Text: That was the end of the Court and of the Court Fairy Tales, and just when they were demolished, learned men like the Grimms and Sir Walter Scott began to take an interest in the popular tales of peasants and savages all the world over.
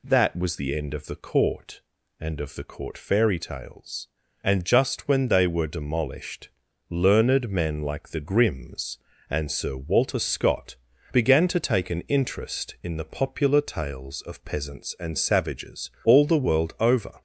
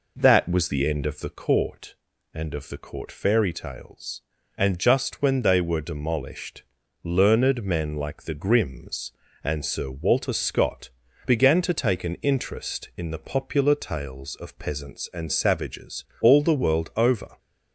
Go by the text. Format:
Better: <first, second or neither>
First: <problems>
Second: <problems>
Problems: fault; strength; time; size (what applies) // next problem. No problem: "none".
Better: first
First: pauses between "Scott" and "began"; at 10.7 s; 0.38 s long // pauses between "savages" and "all"; slight; at 15.8 s; 0.16 s long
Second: starts louder than the rest; noticeable; until 1.4 s; 4.5 dB // pauses between "Scott" and "began"; at 10.8 s; 0.38 s long // pauses between "savages" and "all"; slight; at 16.0 s; 0.18 s long